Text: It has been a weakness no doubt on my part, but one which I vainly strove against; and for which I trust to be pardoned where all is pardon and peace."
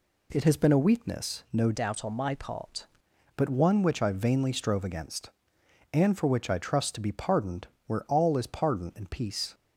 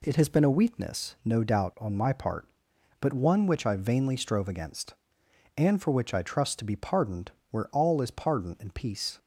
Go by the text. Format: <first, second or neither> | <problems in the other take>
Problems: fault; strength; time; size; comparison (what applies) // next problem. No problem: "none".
second | changes voice from "doubt" to "part"; from 1.7 to 2.8 s; 1.1 s long // pauses between "pardoned" and "where"; slight; at 7.6 s; 0.18 s long; slight in the second